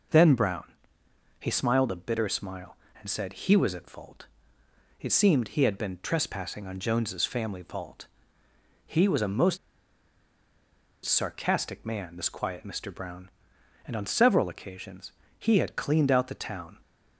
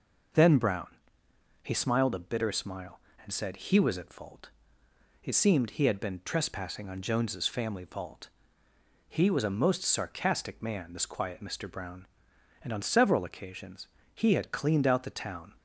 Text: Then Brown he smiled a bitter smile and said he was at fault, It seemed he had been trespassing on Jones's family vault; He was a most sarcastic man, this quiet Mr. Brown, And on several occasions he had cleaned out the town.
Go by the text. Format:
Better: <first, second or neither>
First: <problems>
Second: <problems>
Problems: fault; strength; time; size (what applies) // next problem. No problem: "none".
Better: second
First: pauses between "Brown" and "he"; noticeable; at 0.6 s; 0.76 s long // pauses between "most" and "sarcastic"; strong; at 9.5 s; 1.4 s long // pauses between "occasions" and "he"; slight; at 15.1 s; 0.26 s long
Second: pauses between "Brown" and "he"; noticeable; at 0.8 s; 0.76 s long // pauses between "occasions" and "he"; slight; at 13.8 s; 0.26 s long